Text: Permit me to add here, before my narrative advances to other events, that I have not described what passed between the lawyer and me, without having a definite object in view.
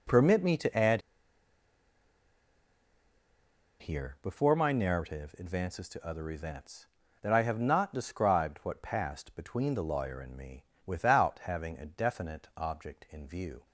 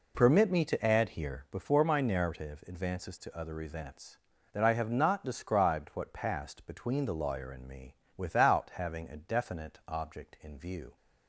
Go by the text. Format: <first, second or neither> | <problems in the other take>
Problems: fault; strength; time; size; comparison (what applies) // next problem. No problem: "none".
second | pauses between "add" and "here"; strong; at 1.0 s; 2.8 s long